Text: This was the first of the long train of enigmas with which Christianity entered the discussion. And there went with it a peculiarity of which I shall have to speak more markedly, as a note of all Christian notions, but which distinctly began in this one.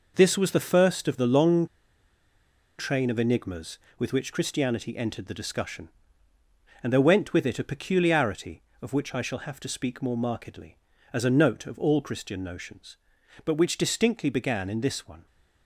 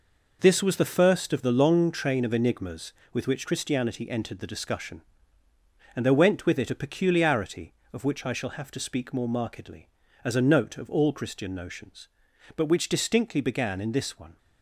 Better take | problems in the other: second | pauses between "long" and "train"; at 1.6 s; 1.1 s long

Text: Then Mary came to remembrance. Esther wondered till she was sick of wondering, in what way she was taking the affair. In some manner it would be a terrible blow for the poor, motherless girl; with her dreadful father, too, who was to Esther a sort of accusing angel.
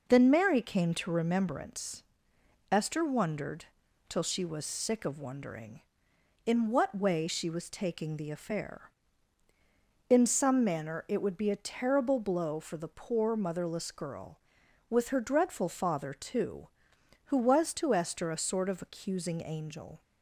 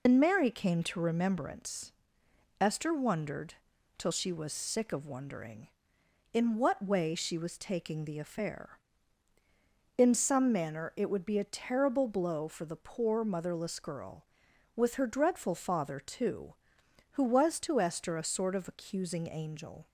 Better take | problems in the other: first | loses the start of "Then"; at 0.0 s; 80 ms // pauses between "wondered" and "till"; at 3.5 s; 0.42 s long; also in the first

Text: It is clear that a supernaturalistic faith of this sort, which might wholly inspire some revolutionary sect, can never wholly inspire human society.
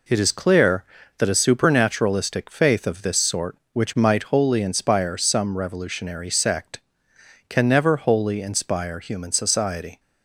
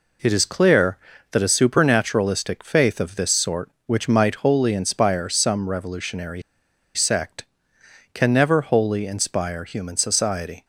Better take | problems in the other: first | pauses between "revolutionary" and "sect"; noticeable; at 6.4 s; 0.53 s long

